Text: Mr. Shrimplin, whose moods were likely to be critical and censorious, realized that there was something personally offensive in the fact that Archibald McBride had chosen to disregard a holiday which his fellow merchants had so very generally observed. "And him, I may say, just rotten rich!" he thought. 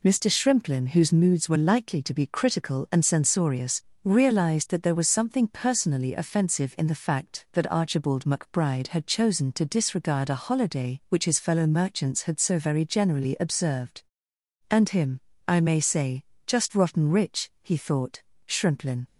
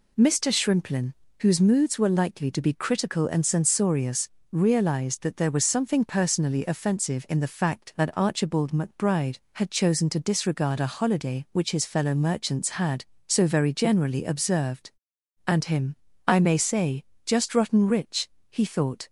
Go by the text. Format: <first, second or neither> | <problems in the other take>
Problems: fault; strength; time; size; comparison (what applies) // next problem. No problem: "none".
second | goes on to say "Shrimplin"; from 18.4 s on; 0.58 s long